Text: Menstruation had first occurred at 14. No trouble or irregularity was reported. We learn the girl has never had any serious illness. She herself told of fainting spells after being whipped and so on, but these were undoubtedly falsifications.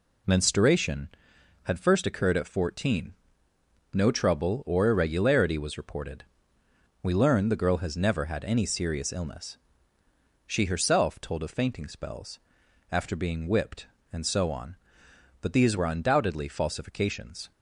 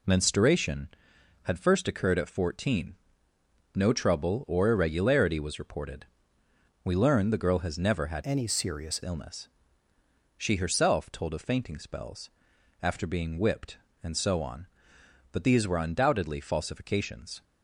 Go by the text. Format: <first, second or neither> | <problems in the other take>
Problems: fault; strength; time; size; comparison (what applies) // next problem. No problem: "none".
first | changes voice from "any" to "serious"; from 8.2 to 9.0 s; 0.8 s long // pauses between "spells" and "after"; noticeable; at 12.2 s; 0.52 s long; noticeable in the first